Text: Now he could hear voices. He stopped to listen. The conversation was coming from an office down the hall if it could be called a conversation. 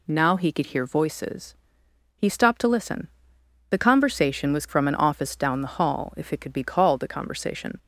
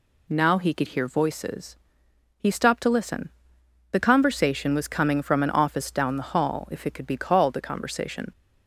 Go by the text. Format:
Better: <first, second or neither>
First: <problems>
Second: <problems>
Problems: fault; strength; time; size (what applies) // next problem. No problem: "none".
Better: second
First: skips "coming"; at 4.6 s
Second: none